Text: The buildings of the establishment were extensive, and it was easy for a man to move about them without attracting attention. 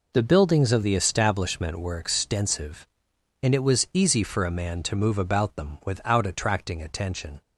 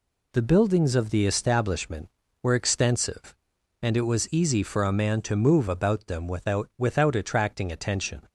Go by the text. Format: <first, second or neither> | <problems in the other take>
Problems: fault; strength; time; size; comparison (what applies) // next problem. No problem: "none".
first | says "without" twice; at 6.7 s